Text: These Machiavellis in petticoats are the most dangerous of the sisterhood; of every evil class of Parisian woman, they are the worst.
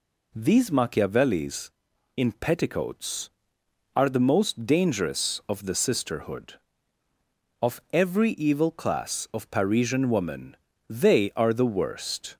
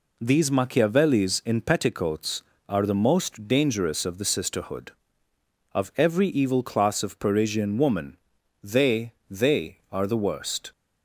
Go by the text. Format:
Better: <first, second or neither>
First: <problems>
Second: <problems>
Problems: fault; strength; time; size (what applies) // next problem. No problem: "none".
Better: first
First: none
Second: says "they" twice; at 9.2 s